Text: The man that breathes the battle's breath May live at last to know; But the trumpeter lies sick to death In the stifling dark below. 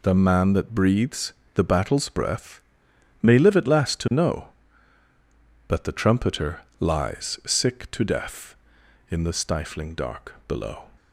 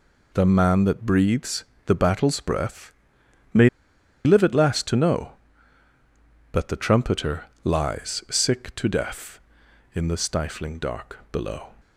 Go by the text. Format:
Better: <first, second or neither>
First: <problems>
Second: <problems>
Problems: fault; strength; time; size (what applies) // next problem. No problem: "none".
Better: first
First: pauses between "breathes" and "the"; slight; at 1.3 s; 0.22 s long // pauses between "breath" and "May"; noticeable; at 2.6 s; 0.60 s long // pauses between "trumpeter" and "lies"; slight; at 6.6 s; 0.18 s long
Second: pauses between "breathes" and "the"; slight; at 1.6 s; 0.22 s long // pauses between "breath" and "May"; noticeable; at 2.9 s; 0.60 s long // pauses between "May" and "live"; noticeable; at 3.6 s; 0.56 s long // pauses between "trumpeter" and "lies"; slight; at 7.4 s; 0.18 s long